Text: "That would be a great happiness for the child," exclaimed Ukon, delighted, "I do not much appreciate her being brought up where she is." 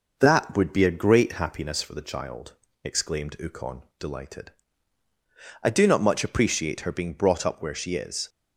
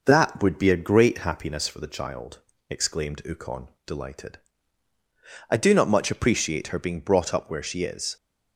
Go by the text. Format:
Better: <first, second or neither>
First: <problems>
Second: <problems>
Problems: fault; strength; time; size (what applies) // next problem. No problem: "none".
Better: neither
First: none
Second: none